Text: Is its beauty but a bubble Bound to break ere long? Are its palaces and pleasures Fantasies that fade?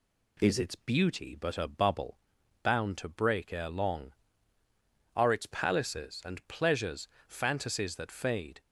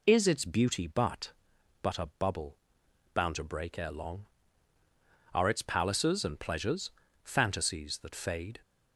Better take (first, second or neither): first